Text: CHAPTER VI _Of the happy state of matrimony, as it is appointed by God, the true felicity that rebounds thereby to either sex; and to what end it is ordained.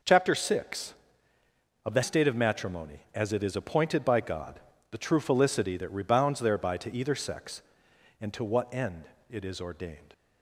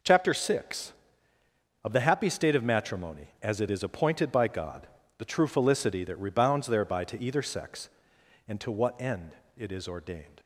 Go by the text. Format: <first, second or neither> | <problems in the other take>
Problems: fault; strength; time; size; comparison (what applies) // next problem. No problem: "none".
second | skips "happy"; at 2.0 s // pauses between "end" and "it"; slight; at 9.0 s; 0.22 s long; slight in the second